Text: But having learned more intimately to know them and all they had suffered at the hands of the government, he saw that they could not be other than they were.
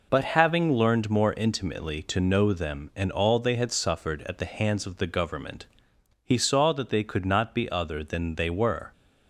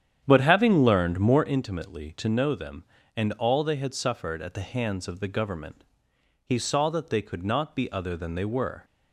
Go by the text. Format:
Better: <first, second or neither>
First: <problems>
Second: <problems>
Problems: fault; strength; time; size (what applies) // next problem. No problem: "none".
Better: first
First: none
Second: starts louder than the rest; strong; until 1.6 s; 9 dB